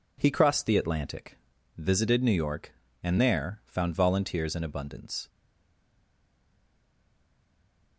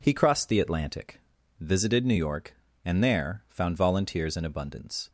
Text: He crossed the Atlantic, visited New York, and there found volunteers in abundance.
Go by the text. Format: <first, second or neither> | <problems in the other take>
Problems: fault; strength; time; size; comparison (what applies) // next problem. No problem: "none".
second | stays silent after the last word; strong; from 5.2 s on; 2.7 s long